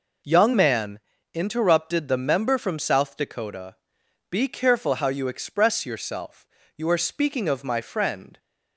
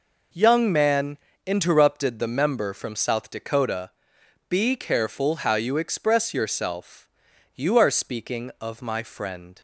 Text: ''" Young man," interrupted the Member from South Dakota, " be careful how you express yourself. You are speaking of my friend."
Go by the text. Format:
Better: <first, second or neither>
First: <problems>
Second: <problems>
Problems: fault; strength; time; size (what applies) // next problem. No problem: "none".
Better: neither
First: none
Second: none